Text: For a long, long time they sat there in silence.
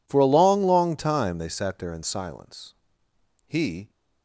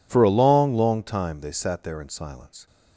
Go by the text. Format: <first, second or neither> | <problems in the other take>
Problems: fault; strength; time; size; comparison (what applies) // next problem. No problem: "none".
second | goes on to say "He"; slight; from 3.4 s on; 0.42 s long